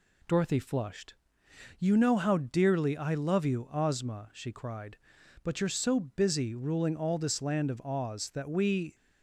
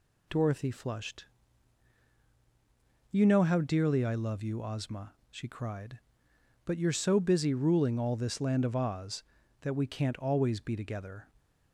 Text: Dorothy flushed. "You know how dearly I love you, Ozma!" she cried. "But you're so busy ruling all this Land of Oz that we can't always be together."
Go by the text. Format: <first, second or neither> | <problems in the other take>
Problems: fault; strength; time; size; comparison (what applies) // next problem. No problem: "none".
second | stops before "can't always be together"; at 8.9 s